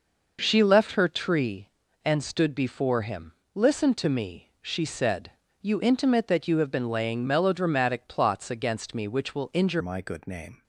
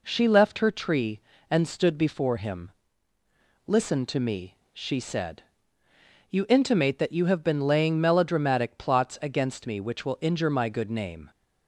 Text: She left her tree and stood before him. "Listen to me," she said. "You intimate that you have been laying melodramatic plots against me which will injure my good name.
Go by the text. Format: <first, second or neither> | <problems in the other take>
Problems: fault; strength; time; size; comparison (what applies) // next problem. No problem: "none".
second | changes voice at "my"; from 9.7 s on; 0.9 s long